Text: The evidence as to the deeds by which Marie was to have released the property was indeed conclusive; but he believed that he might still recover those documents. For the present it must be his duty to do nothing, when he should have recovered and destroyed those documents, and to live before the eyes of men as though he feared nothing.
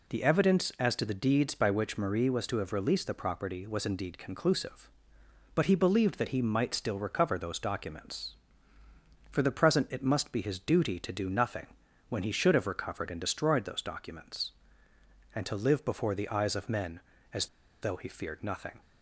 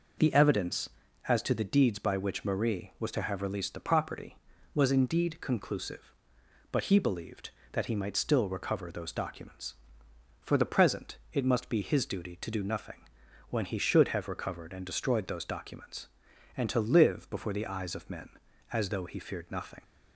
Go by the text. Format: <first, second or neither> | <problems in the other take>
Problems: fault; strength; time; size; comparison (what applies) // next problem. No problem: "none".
second | pauses between "as" and "though"; slight; at 17.4 s; 0.35 s long